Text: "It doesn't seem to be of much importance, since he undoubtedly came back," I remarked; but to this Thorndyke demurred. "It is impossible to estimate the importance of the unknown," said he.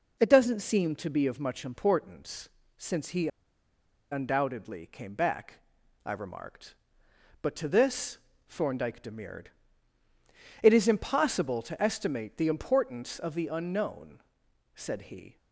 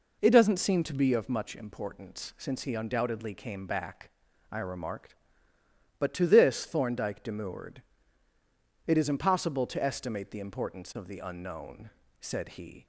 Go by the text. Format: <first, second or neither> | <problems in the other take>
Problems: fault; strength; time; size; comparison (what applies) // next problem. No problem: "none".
second | pauses between "he" and "undoubtedly"; noticeable; at 3.2 s; 0.83 s long // pauses between "this" and "Thorndyke"; slight; at 8.1 s; 0.32 s long